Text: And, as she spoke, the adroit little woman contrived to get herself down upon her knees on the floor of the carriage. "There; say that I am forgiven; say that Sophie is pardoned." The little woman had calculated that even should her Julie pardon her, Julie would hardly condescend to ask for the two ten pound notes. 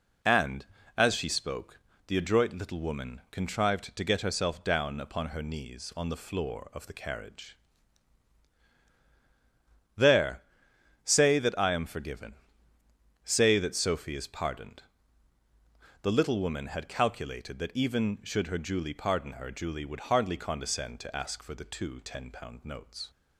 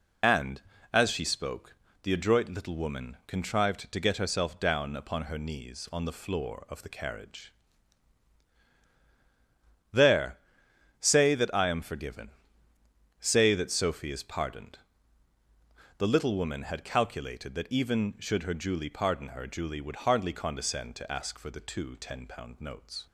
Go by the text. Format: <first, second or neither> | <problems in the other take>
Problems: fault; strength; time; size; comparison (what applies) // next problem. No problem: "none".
first | loses the start of "And"; at 0.2 s; 35 ms